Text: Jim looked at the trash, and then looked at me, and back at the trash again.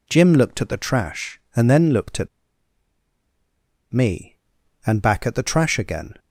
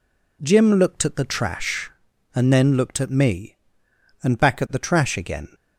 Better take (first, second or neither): second